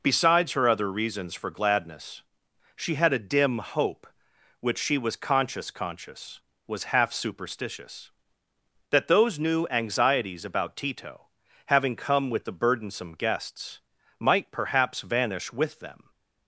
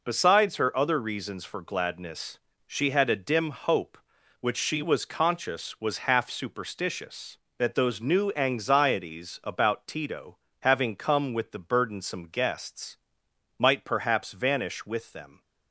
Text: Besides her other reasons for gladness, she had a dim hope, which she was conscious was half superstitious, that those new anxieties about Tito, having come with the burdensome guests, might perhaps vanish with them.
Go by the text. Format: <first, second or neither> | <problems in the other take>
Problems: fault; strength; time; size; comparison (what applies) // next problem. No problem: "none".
second | says "conscious" twice; at 5.7 s